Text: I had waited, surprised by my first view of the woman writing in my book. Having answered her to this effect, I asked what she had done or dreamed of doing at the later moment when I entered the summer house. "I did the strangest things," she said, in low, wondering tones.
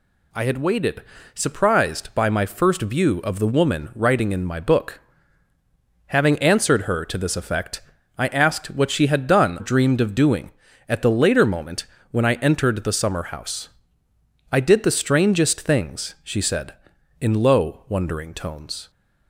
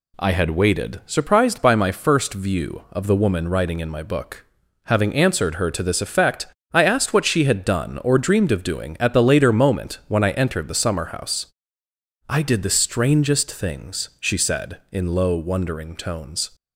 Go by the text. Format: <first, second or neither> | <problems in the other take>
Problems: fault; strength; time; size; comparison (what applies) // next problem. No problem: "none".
second | skips "or"; at 9.5 s // pauses between "moment" and "when"; slight; at 11.8 s; 0.24 s long